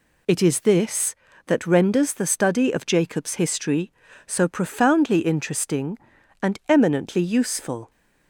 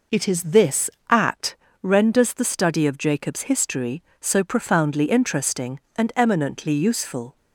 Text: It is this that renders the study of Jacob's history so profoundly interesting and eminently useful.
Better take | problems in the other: first | says "at" for "that"; at 1.0 s

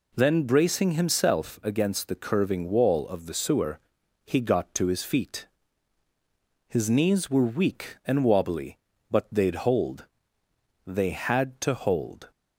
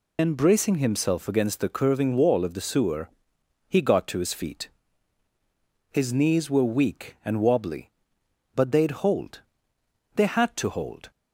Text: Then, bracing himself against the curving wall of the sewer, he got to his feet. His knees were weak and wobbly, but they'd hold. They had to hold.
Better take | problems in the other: first | loses the start of "Then"; at 0.1 s; 145 ms

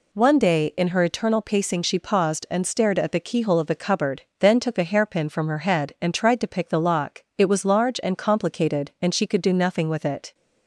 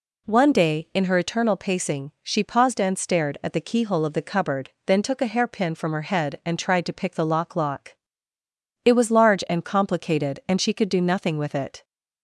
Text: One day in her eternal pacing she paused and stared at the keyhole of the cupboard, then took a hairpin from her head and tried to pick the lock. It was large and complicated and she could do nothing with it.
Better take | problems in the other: first | says "lock" twice; at 7.5 s

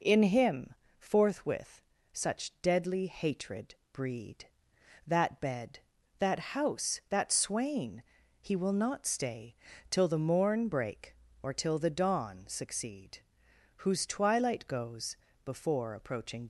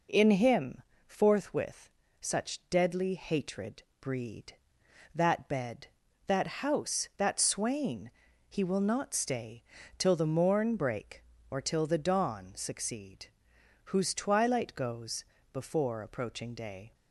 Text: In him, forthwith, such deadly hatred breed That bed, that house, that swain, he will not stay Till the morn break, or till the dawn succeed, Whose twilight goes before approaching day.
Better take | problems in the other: second | pauses between "hatred" and "breed"; slight; at 3.7 s; 0.18 s long; slight in the second // pauses between "stay" and "Till"; at 9.5 s; 0.38 s long; also in the second // pauses between "goes" and "before"; slight; at 15.1 s; 0.30 s long; slight in the second // stops before "day"; at 16.4 s

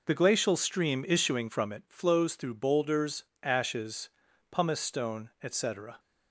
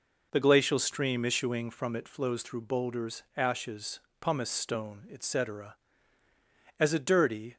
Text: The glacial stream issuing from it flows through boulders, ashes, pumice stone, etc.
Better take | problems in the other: first | goes on to say "as a dirty"; noticeable; from 6.7 s on; 0.78 s long

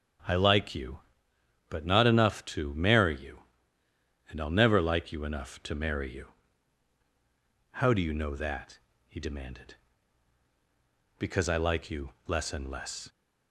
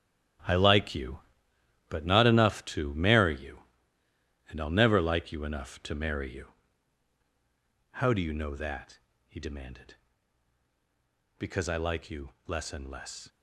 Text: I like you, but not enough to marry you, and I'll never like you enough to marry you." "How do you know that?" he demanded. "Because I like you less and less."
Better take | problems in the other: first | gets quieter; strong; throughout; 11.5 dB // starts louder than the rest; strong; until 2.1 s; 11.5 dB; strong in the first

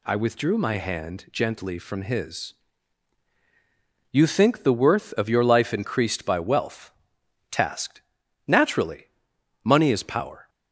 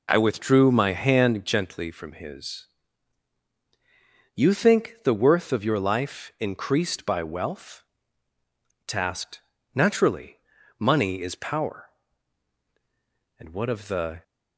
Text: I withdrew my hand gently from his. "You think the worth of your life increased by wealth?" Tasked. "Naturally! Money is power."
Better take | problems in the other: first | goes on to say "And what of the"; noticeable; from 13.3 s on; 0.86 s long

